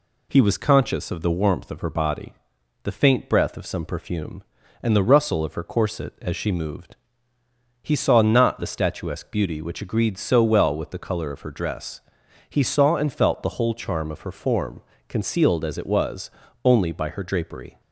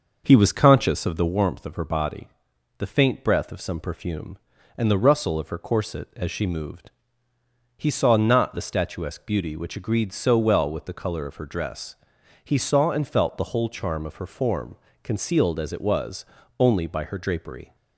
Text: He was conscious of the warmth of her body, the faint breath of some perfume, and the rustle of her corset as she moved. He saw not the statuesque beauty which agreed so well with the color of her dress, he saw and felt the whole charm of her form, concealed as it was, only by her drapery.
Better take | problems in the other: first | starts louder than the rest; noticeable; until 1.3 s; 6 dB

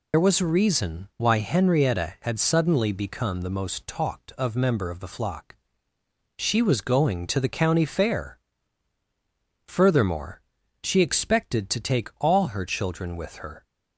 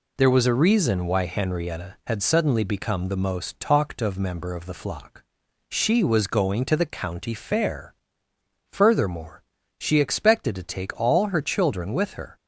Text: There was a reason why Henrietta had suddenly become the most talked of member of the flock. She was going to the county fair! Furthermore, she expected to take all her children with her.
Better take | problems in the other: second | loses the start of "There"; at 0.1 s; 50 ms

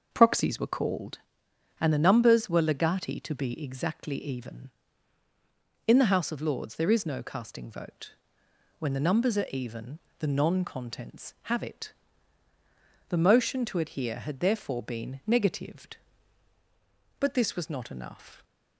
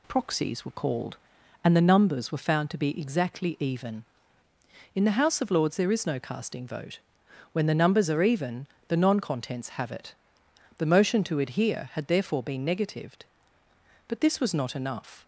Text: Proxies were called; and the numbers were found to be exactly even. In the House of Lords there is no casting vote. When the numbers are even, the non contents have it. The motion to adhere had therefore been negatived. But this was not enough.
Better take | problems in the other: second | starts louder than the rest; until 1.1 s; 6 dB // says "legati" for "found"; at 2.6 s

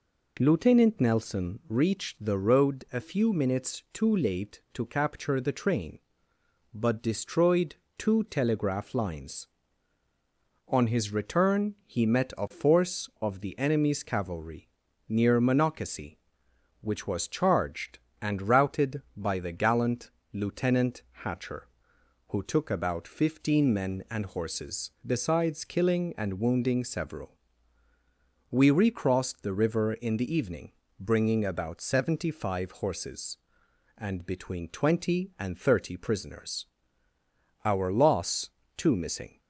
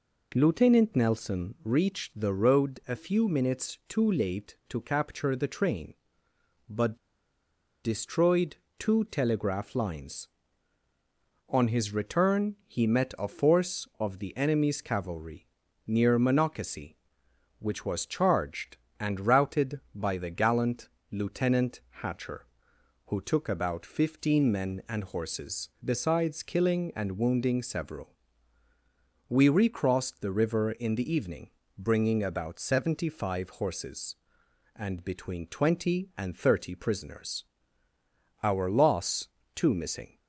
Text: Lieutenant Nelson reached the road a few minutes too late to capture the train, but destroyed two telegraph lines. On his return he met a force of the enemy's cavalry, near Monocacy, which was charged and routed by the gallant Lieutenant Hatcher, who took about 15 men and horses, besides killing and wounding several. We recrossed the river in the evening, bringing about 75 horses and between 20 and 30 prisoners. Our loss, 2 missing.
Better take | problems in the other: first | pauses between "but" and "destroyed"; noticeable; at 6.9 s; 0.86 s long // pauses between "destroyed" and "two"; slight; at 8.5 s; 0.24 s long; slight in the first // pauses between "gallant" and "Lieutenant"; slight; at 20.8 s; 0.22 s long; slight in the first // pauses between "Lieutenant" and "Hatcher"; slight; at 21.8 s; 0.20 s long; slight in the first

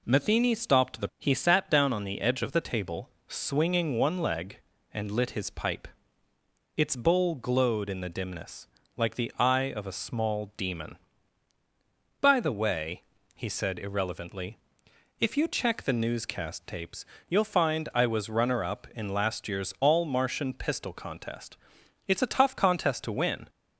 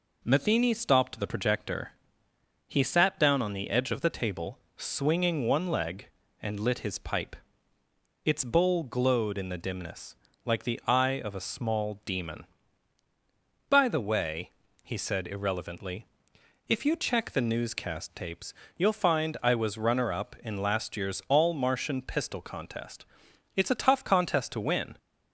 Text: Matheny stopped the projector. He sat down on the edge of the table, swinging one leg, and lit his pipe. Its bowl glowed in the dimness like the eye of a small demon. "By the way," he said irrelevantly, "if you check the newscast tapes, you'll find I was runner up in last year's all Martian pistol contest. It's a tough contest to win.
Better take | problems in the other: second | skips "projector"; at 1.1 s // pauses between "dimness" and "like"; slight; at 8.6 s; 0.28 s long; slight in the second

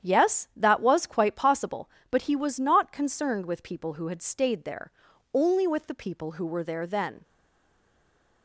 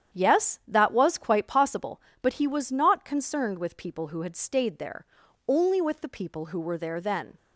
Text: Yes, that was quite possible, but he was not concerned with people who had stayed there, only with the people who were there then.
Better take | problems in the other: second | starts louder than the rest; strong; until 1.1 s; 9.5 dB; strong in the second // stays silent after the last word; noticeable; from 7.2 s on; 1.2 s long

